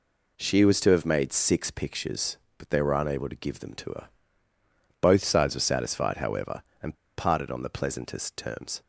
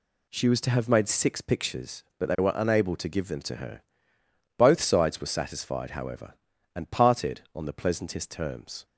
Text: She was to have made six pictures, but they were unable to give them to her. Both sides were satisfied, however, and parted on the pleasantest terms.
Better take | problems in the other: second | pauses between "and" and "parted"; slight; at 6.9 s; 0.22 s long

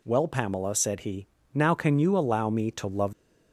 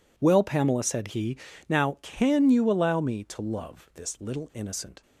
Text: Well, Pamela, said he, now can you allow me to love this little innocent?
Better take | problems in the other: second | stops before "this little innocent"; at 3.1 s

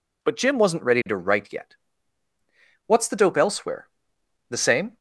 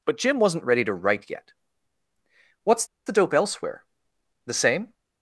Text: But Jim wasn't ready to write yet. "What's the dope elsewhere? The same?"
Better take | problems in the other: first | pauses between "What's" and "the"; slight; at 2.8 s; 0.20 s long

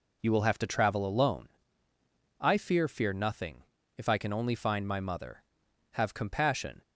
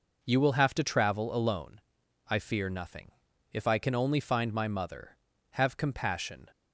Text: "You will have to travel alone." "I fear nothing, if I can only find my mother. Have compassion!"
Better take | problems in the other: second | says "fear" twice; at 2.8 s

